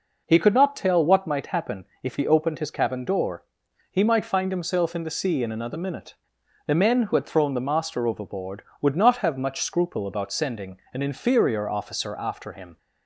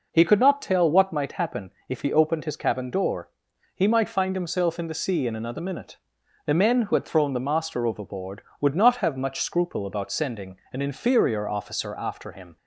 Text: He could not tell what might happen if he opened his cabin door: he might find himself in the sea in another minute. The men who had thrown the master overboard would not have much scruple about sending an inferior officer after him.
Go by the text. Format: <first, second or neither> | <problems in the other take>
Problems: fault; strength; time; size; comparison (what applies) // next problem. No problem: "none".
neither | pauses between "happen" and "if"; slight; the same in both